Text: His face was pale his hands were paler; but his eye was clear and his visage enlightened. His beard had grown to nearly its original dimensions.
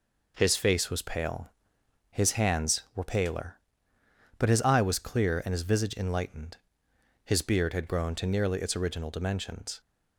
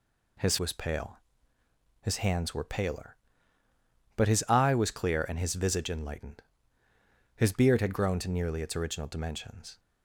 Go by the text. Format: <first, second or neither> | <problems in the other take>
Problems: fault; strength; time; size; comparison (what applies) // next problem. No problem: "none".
first | skips "face"; at 0.5 s // pauses between "pale" and "his"; noticeable; at 1.1 s; 0.84 s long; noticeable in the first